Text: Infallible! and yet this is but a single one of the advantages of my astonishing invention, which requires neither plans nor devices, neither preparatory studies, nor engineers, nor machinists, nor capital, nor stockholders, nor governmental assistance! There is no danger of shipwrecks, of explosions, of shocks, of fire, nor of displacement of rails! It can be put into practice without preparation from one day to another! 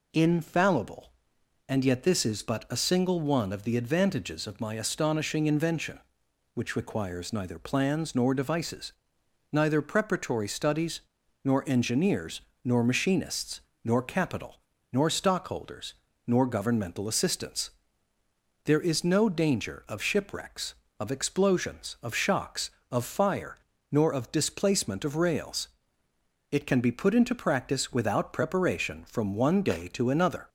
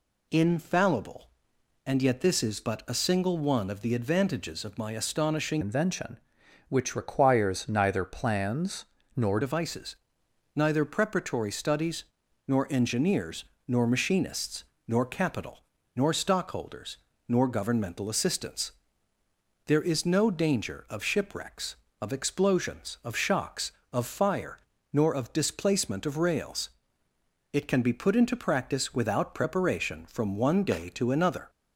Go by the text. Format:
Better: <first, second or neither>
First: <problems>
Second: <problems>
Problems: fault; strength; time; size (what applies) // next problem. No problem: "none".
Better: first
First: none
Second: changes voice from "invention" to "nor"; from 5.6 to 9.3 s; 3.7 s long // pauses between "plans" and "nor"; slight; at 8.8 s; 0.30 s long